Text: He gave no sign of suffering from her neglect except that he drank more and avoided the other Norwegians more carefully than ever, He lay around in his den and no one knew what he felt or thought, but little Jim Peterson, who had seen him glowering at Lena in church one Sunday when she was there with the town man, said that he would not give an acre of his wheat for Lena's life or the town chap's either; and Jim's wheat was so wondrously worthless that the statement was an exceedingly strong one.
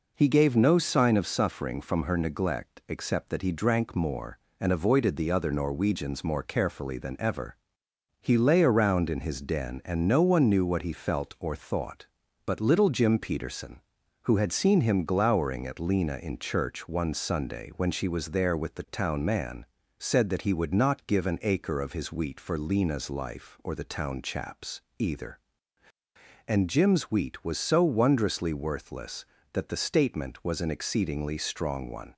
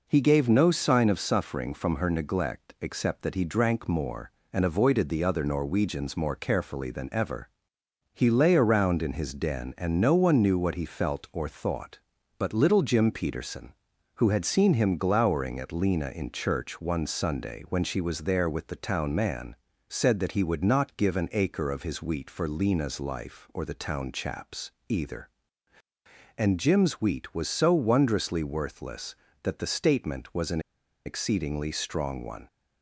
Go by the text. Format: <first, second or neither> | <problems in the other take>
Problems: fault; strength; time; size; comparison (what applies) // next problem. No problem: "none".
first | pauses between "chap's" and "either"; slight; at 24.7 s; 0.18 s long; slight in the first // pauses between "an" and "exceedingly"; noticeable; at 30.5 s; 0.46 s long